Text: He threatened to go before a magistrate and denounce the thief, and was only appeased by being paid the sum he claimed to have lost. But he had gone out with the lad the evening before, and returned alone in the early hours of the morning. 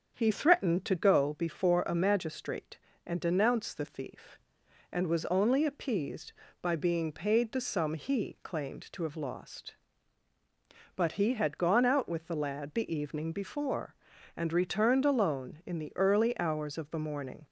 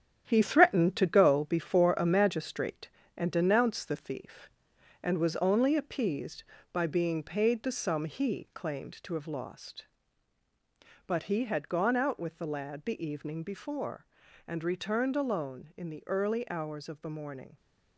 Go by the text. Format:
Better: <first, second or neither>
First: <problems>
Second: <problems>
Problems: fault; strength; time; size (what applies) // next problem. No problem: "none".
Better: first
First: starts louder than the rest; until 1.1 s; 6.5 dB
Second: gets quieter; throughout; 6.5 dB // starts louder than the rest; strong; until 1.2 s; 9 dB